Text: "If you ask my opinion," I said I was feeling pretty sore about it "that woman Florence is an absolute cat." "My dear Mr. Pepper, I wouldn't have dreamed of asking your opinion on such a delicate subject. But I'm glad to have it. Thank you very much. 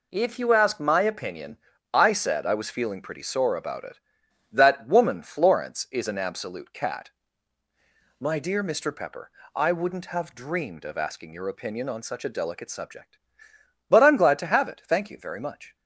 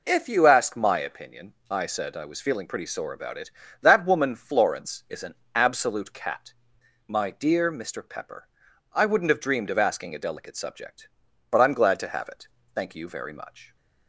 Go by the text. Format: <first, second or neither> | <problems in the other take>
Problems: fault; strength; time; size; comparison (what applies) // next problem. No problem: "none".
first | pauses between "an" and "absolute"; slight; at 5.3 s; 0.18 s long // skips "your opinion on such"; at 10.1 s